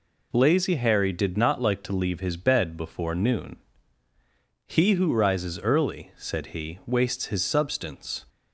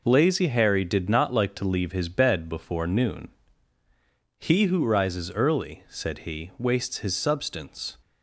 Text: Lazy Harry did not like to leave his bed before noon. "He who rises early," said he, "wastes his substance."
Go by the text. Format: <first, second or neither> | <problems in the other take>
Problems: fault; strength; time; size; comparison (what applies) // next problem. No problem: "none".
first | gets quieter; strong; throughout; 7.5 dB